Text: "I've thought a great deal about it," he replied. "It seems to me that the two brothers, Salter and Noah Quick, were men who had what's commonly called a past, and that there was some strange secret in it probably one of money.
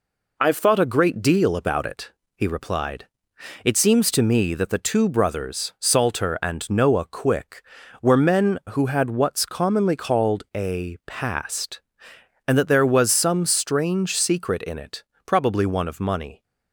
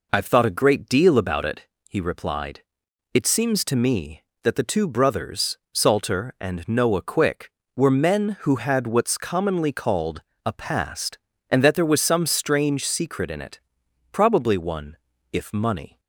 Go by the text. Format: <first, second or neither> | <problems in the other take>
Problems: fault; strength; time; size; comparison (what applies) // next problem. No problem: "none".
first | pauses between "called" and "a"; slight; at 10.2 s; 0.24 s long // pauses between "it" and "probably"; noticeable; at 13.5 s; 0.52 s long; slight in the first // says "if" for "of"; at 15.3 s